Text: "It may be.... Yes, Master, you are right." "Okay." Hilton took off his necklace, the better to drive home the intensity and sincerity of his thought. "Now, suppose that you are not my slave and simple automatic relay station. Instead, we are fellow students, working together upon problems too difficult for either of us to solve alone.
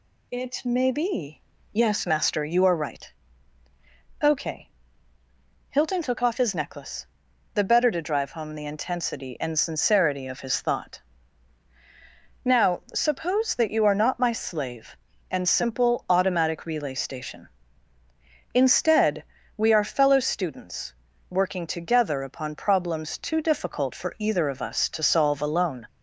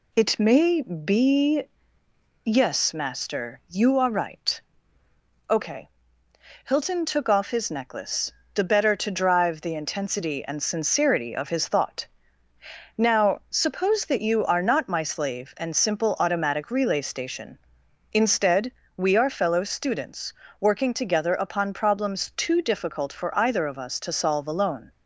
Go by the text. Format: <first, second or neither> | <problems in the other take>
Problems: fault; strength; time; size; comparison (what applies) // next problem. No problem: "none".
first | skips "home"; at 9.6 s